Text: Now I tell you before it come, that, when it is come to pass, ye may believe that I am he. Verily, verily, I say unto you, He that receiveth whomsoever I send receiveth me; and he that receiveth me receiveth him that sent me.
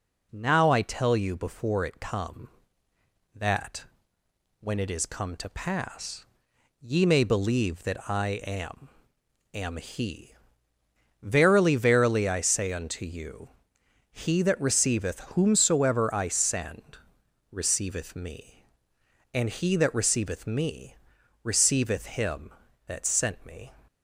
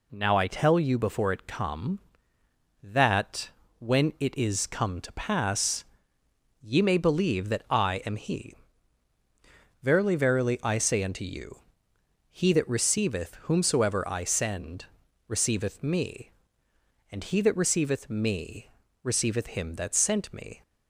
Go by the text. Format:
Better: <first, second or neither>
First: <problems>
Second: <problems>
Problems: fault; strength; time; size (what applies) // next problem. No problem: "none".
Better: second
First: says "am" twice; at 9.5 s // pauses between "send" and "receiveth"; noticeable; at 16.9 s; 0.52 s long // pauses between "me" and "receiveth"; noticeable; at 20.9 s; 0.46 s long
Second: pauses between "send" and "receiveth"; at 14.8 s; 0.42 s long // pauses between "me" and "receiveth"; slight; at 18.6 s; 0.34 s long